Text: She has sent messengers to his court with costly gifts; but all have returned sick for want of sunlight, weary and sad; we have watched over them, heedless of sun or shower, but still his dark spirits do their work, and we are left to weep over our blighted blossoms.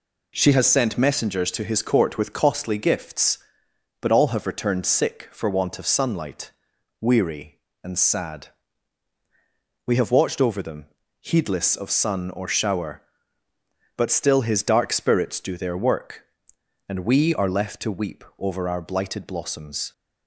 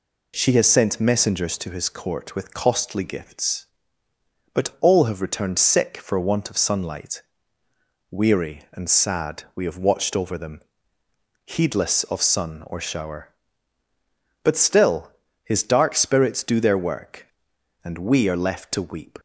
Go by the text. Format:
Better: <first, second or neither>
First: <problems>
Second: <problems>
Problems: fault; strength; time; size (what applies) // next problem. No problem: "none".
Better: first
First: none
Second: pauses between "still" and "his"; slight; at 15.1 s; 0.32 s long // stops before "over our blighted blossoms"; at 19.1 s